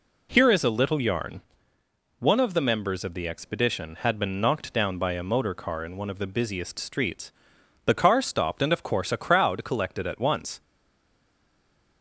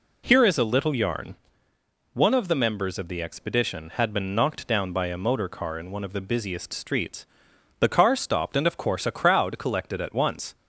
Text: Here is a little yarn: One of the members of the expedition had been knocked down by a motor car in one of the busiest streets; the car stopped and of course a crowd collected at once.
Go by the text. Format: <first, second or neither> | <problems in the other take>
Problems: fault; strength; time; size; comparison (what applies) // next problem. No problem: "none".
second | stays silent after the last word; noticeable; from 10.6 s on; 1.4 s long